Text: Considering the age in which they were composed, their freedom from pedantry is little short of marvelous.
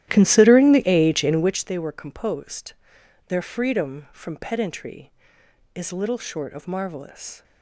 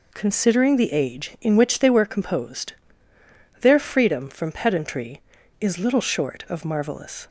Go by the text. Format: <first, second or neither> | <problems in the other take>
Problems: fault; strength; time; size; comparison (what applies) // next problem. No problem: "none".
second | starts louder than the rest; strong; until 1.7 s; 13.5 dB